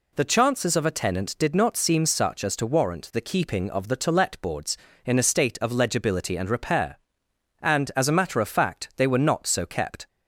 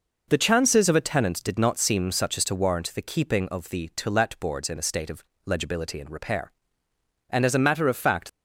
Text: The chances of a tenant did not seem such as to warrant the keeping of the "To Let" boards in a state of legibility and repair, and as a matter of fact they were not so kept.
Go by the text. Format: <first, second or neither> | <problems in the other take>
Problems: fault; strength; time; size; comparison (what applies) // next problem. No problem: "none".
first | pauses between "of" and "legibility"; slight; at 5.2 s; 0.24 s long // stops before "they were not so kept"; at 8.2 s